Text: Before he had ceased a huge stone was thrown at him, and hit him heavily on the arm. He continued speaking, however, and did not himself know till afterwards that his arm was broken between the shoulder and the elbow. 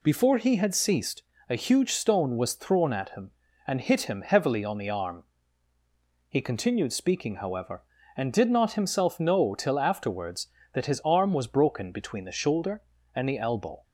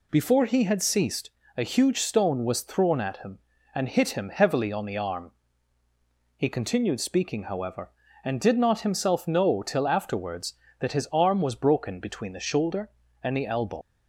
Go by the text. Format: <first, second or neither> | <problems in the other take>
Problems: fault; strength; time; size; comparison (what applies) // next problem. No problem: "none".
first | pauses between "ceased" and "a"; slight; at 1.2 s; 0.26 s long; slight in the first // leaves "elbow" unfinished; at 13.8 s; 100 ms